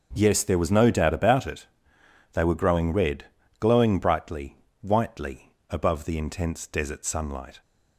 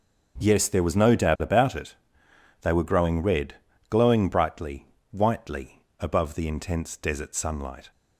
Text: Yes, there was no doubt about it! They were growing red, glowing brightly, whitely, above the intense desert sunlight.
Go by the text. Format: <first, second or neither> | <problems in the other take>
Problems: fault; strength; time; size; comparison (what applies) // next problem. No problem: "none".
neither | starts louder than the rest; the same in both